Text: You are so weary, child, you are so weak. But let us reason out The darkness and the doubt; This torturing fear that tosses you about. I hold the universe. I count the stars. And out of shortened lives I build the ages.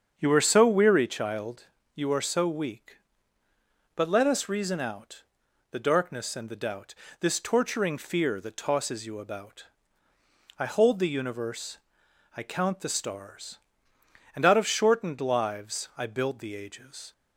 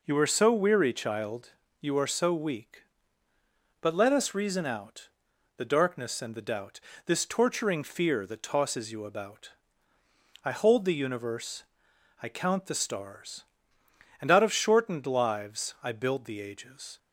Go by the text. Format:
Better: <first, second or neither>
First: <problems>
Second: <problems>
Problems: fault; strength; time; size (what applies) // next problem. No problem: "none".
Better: second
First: starts louder than the rest; strong; until 1.1 s; 7 dB // pauses between "out" and "The"; noticeable; at 5.2 s; 0.48 s long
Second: pauses between "out" and "The"; noticeable; at 5.0 s; 0.48 s long